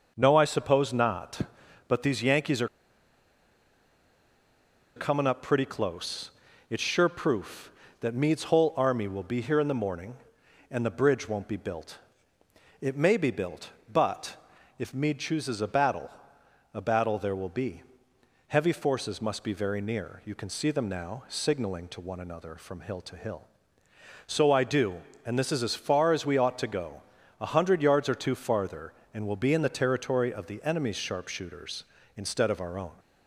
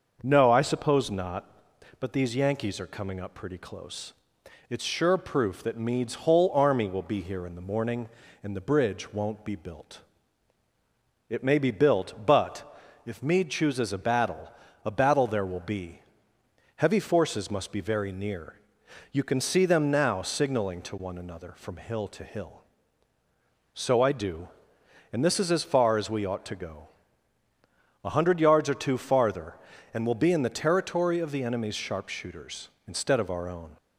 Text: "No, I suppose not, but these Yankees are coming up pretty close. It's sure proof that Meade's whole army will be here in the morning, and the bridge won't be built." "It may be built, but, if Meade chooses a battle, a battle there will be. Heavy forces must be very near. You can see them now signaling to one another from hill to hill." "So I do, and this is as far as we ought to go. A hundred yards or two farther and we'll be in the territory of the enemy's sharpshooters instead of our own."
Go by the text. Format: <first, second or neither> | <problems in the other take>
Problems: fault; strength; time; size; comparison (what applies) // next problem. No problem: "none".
second | starts louder than the rest; until 1.1 s; 6.5 dB; noticeable in the second // pauses between "are" and "coming"; strong; at 2.6 s; 2.2 s long